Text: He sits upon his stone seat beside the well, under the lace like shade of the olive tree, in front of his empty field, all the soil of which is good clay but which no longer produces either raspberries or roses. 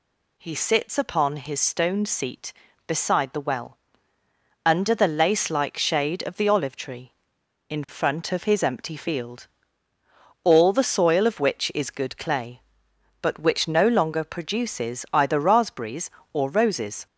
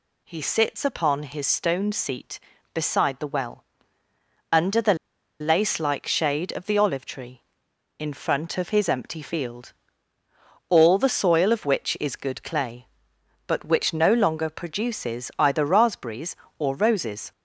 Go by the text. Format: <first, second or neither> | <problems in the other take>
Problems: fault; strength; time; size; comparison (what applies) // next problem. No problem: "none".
first | pauses between "the" and "lace"; at 4.9 s; 0.45 s long